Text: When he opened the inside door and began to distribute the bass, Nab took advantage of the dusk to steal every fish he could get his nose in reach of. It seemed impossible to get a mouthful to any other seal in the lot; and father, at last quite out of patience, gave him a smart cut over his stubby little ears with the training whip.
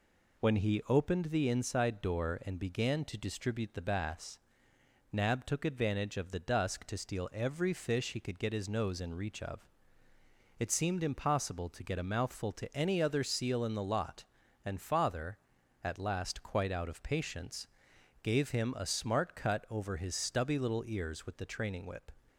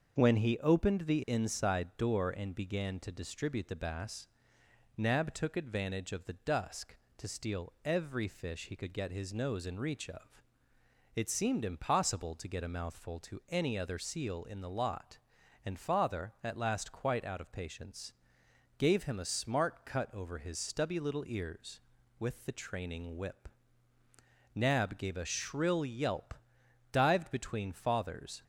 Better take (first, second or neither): first